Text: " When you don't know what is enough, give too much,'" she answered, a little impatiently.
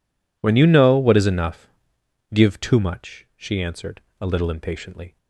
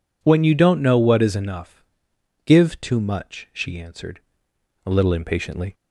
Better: second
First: skips "don't"; at 0.6 s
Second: none

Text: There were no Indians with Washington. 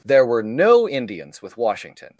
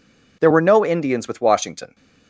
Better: neither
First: none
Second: none

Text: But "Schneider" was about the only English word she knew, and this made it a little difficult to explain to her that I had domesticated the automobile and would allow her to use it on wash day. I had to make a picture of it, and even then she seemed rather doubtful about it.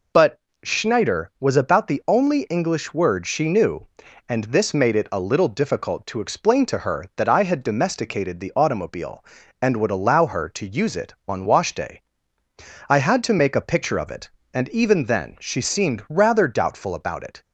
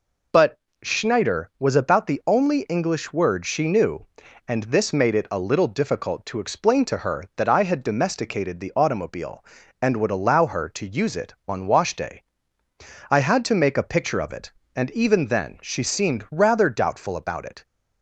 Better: neither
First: pauses between "But" and "Schneider"; slight; at 0.3 s; 0.24 s long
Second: pauses between "But" and "Schneider"; slight; at 0.5 s; 0.24 s long

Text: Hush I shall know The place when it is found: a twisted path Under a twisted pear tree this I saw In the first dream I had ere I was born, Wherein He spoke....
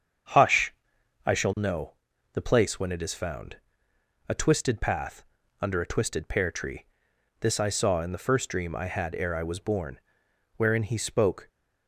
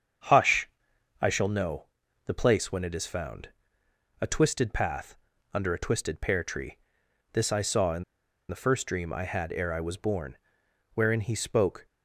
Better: first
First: starts louder than the rest; strong; until 1.8 s; 7.5 dB // pauses between "Hush" and "I"; noticeable; at 0.7 s; 0.52 s long // pauses between "know" and "The"; at 1.9 s; 0.40 s long // pauses between "path" and "Under"; at 5.2 s; 0.38 s long // pauses between "tree" and "this"; noticeable; at 6.8 s; 0.56 s long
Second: starts louder than the rest; strong; until 1.7 s; 7.5 dB // pauses between "Hush" and "I"; noticeable; at 0.6 s; 0.52 s long // pauses between "know" and "The"; at 1.8 s; 0.40 s long // pauses between "path" and "Under"; at 5.1 s; 0.38 s long // pauses between "tree" and "this"; noticeable; at 6.7 s; 0.56 s long // pauses between "In" and "the"; at 8.0 s; 0.45 s long

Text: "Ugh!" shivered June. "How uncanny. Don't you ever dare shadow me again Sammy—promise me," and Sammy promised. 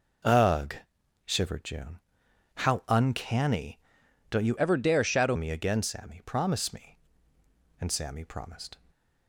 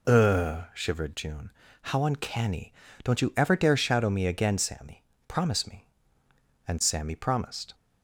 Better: second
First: changes voice from "ever" to "shadow"; from 4.5 to 5.3 s; 0.8 s long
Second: none

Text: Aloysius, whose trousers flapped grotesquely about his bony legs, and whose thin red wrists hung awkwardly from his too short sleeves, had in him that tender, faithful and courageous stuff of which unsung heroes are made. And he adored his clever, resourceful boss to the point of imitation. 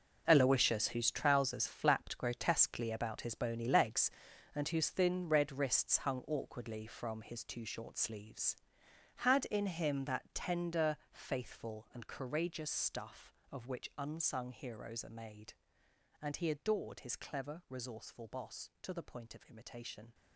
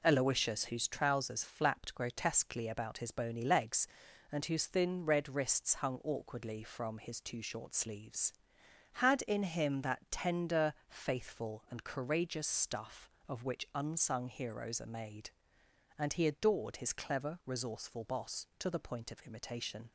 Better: second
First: gets quieter; strong; throughout; 13 dB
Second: none

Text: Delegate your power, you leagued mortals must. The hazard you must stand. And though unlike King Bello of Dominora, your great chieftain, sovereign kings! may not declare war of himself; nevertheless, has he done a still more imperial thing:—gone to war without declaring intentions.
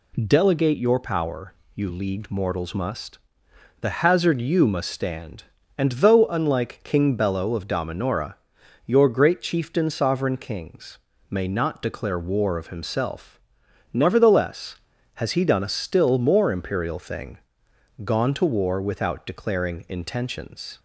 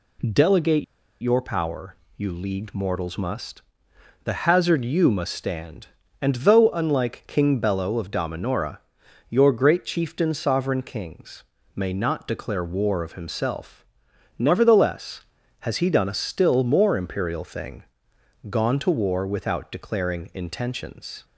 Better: first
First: none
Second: pauses between "Delegate" and "your"; at 0.8 s; 0.36 s long

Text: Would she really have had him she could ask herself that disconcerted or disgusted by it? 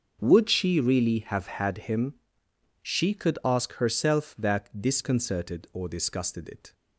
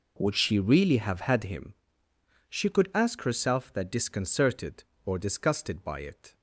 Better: second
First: starts louder than the rest; until 1.2 s; 6.5 dB // pauses between "him" and "she"; noticeable; at 2.1 s; 0.66 s long // skips "by"; at 6.4 s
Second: pauses between "him" and "she"; noticeable; at 1.7 s; 0.76 s long

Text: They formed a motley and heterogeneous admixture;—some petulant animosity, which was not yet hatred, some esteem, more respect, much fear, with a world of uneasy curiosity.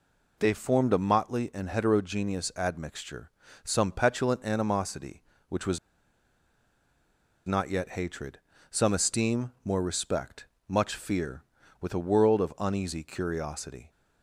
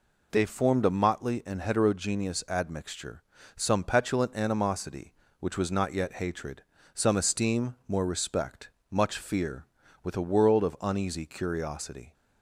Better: second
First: pauses between "was" and "not"; strong; at 5.7 s; 1.6 s long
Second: none

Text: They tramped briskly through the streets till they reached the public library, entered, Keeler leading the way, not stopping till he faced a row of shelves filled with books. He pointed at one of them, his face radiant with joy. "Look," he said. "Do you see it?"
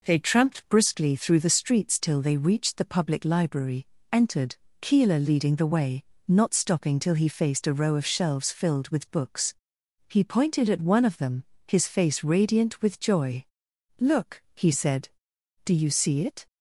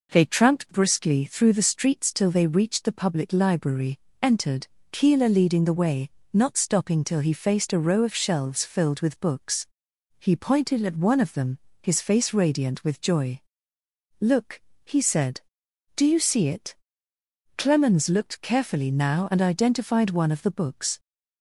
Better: first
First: none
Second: goes on to say "Clemens looked carefully now and identified one of the books"; strong; from 17.5 s on; 3.4 s long

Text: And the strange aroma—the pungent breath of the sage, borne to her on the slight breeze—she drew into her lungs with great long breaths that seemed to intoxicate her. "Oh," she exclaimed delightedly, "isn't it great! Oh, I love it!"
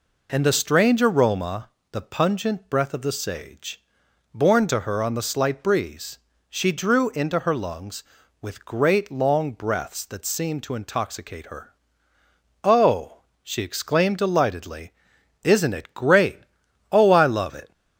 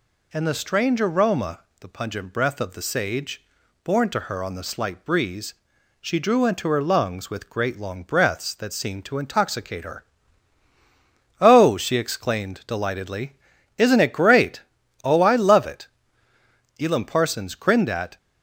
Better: first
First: none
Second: goes on to say "Elam Parsons grinned at"; from 16.7 s on; 1.3 s long

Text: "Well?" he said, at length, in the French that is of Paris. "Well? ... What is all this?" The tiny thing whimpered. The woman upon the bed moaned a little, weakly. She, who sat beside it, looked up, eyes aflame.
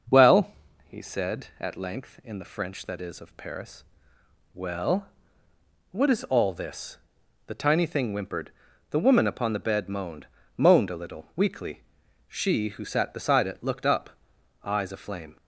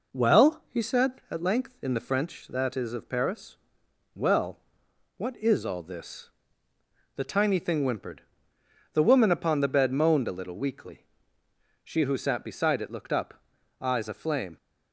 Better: second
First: starts louder than the rest; noticeable; until 1.4 s; 6 dB // says "moaned" twice; at 10.5 s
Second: none

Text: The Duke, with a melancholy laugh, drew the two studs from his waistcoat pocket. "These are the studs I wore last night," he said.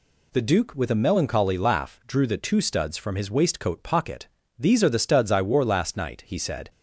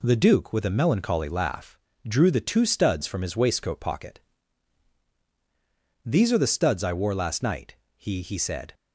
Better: first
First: none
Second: says "he" twice; at 8.2 s

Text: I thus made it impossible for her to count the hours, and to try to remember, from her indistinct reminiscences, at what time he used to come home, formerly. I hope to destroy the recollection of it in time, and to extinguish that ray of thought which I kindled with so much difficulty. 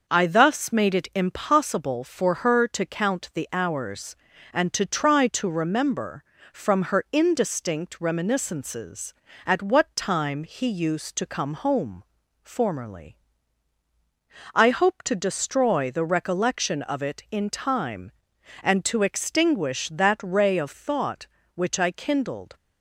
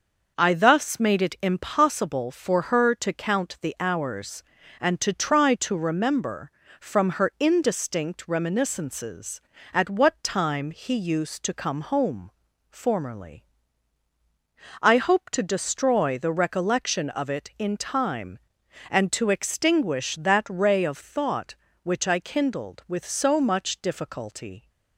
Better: second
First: starts louder than the rest; noticeable; until 1.0 s; 6 dB // stops before "with so much difficulty"; at 22.5 s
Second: starts louder than the rest; noticeable; until 1.3 s; 6 dB

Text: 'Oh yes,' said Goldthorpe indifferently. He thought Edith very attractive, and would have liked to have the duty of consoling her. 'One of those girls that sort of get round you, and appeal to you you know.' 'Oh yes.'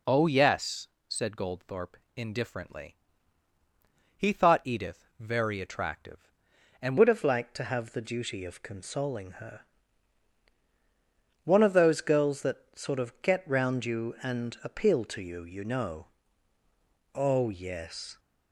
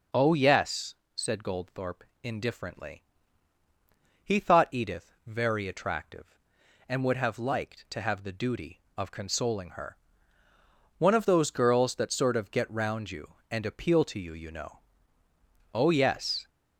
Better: second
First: pauses between "Goldthorpe" and "indifferently"; slight; at 1.9 s; 0.18 s long // changes voice at "would"; from 6.9 s on; 11.2 s long // pauses between "that" and "sort"; slight; at 12.5 s; 0.18 s long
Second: pauses between "Goldthorpe" and "indifferently"; slight; at 2.0 s; 0.18 s long

